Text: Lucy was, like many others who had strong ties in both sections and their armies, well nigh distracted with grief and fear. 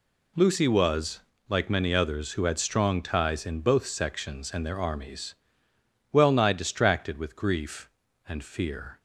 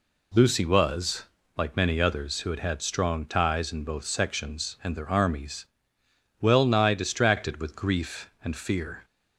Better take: first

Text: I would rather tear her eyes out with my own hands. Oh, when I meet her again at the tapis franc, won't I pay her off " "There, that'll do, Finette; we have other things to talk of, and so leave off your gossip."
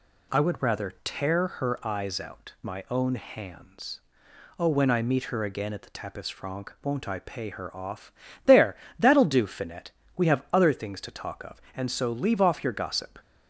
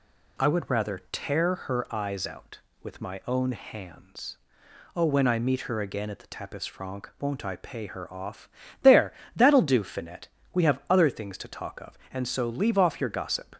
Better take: second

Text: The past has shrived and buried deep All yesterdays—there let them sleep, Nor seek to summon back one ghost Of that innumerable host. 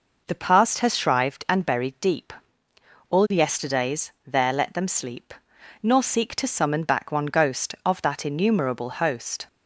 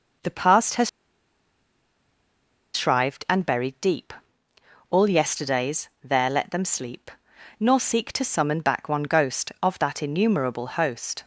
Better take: first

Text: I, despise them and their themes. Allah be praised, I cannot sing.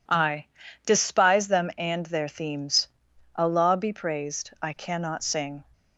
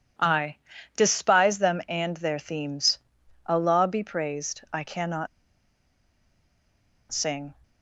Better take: first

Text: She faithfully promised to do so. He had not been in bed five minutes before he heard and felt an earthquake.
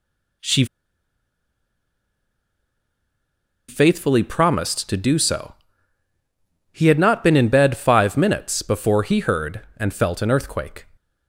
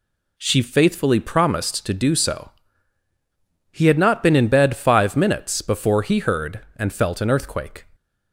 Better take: second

